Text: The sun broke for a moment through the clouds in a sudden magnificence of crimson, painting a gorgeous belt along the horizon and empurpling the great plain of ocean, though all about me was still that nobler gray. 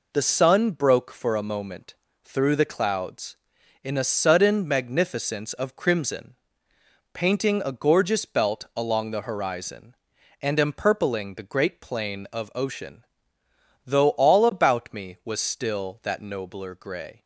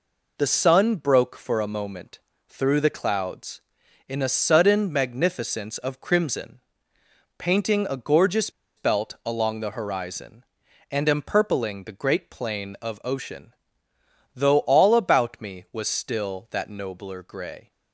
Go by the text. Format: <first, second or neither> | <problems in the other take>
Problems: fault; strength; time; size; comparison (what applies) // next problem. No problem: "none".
first | pauses between "moment" and "through"; slight; at 2.1 s; 0.32 s long; slight in the first // pauses between "gorgeous" and "belt"; slight; at 8.4 s; 0.27 s long